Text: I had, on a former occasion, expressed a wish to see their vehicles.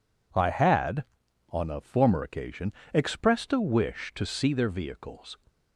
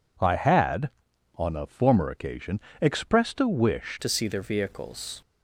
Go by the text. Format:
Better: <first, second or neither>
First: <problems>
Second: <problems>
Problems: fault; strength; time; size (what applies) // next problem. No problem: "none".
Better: first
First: none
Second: changes voice at "to"; from 4.0 s on; 1.2 s long